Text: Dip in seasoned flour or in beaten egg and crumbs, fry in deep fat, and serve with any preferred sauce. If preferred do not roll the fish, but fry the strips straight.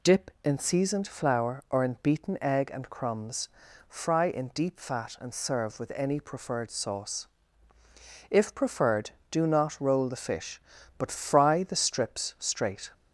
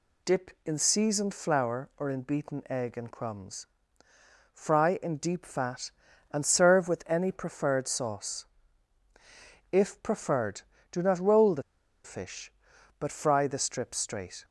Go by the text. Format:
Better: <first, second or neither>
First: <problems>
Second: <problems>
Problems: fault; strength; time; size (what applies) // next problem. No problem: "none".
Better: first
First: none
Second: pauses between "the" and "fish"; at 11.6 s; 0.42 s long